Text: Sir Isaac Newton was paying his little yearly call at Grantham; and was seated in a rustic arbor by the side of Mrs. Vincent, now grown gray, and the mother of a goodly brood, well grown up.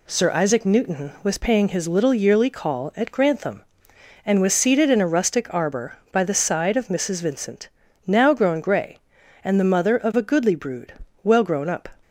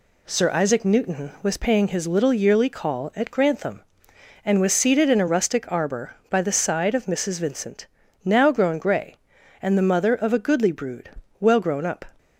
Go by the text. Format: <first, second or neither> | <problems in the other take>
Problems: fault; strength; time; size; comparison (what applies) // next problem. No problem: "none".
neither | none